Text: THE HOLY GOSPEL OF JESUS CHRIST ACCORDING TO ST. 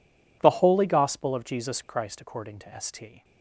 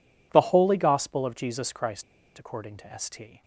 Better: first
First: none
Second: pauses between "CHRIST" and "ACCORDING"; slight; at 2.0 s; 0.34 s long

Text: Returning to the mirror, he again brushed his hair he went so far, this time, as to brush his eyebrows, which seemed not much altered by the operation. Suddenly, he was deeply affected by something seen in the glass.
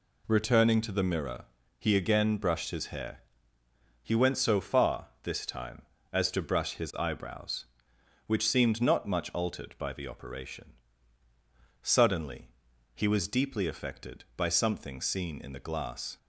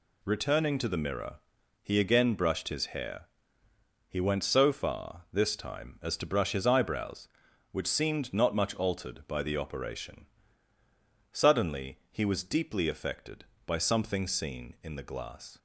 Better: neither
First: pauses between "hair" and "he"; noticeable; at 3.1 s; 0.82 s long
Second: pauses between "hair" and "he"; noticeable; at 3.2 s; 0.86 s long

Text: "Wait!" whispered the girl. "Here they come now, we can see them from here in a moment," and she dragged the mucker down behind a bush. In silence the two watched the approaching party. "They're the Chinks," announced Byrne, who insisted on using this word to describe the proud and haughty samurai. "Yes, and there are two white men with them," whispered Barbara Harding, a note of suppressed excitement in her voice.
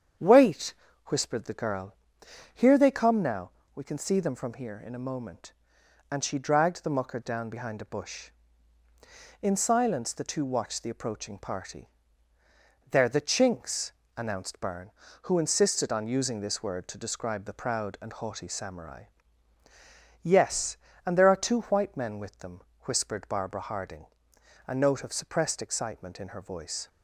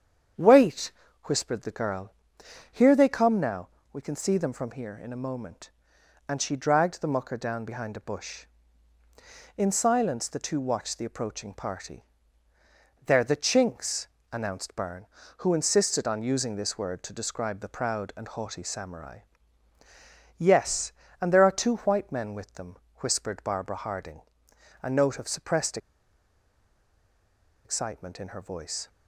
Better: first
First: starts louder than the rest; strong; until 1.5 s; 8 dB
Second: starts louder than the rest; strong; until 1.7 s; 8 dB // pauses between "suppressed" and "excitement"; strong; at 25.7 s; 1.8 s long

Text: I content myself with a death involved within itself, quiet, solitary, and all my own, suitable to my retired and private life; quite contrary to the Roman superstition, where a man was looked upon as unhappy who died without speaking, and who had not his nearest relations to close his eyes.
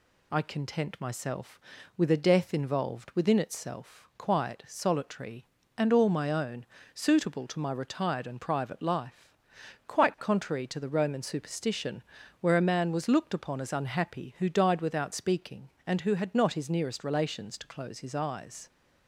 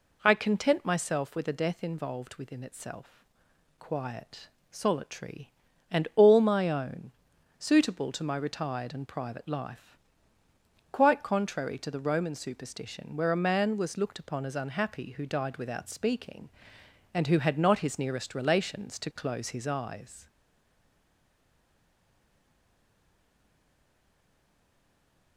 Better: first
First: none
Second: stays silent after the last word; strong; from 20.2 s on; 5.1 s long

